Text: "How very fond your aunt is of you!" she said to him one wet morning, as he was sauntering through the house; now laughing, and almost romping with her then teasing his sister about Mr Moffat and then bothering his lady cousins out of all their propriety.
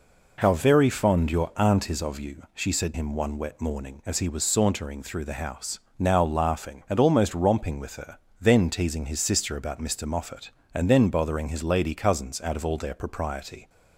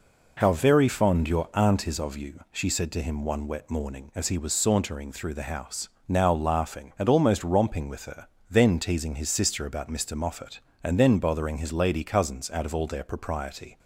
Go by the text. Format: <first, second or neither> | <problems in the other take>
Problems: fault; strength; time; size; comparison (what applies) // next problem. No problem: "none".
second | skips "to"; at 2.9 s // pauses between "her" and "then"; slight; at 8.1 s; 0.22 s long; slight in the second